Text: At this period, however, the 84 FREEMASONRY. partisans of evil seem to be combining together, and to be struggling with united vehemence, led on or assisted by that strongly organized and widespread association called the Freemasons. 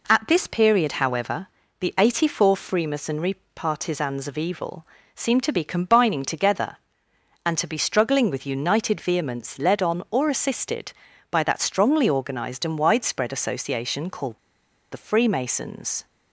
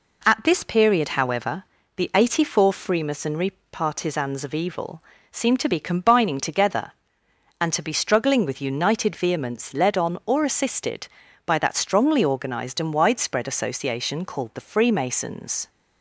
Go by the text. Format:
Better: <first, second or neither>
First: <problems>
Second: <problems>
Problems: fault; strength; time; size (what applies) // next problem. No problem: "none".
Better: second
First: pauses between "evil" and "seem"; slight; at 4.8 s; 0.30 s long // pauses between "called" and "the"; noticeable; at 14.3 s; 0.53 s long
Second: pauses between "evil" and "seem"; slight; at 5.0 s; 0.30 s long